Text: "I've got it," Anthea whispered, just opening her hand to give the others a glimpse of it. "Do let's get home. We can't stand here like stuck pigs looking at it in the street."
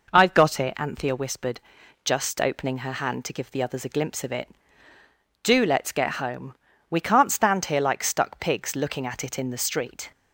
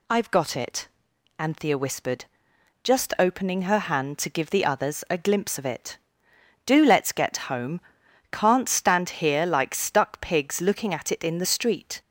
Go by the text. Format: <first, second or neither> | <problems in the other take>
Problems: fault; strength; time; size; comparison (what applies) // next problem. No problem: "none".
first | skips "We"; at 8.0 s